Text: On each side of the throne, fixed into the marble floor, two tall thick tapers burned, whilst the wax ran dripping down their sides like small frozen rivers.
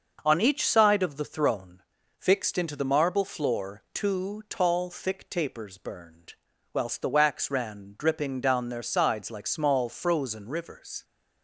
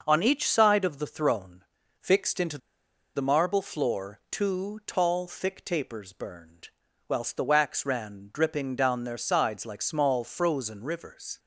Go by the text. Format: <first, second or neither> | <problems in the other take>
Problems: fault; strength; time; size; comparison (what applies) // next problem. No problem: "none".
first | pauses between "into" and "the"; noticeable; at 2.5 s; 0.57 s long